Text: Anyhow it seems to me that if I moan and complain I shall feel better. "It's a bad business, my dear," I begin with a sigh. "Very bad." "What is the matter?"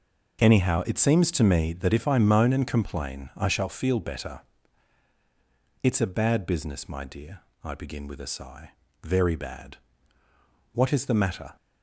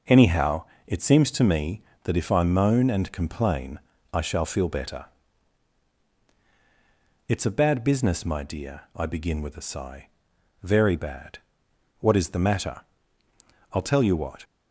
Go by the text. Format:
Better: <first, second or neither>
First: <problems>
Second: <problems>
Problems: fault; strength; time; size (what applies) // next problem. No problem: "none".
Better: first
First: none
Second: pauses between "Anyhow" and "it"; slight; at 0.6 s; 0.22 s long // pauses between "complain" and "I"; slight; at 3.7 s; 0.32 s long // goes on to say "I'll tell you what"; noticeable; from 13.7 s on; 0.72 s long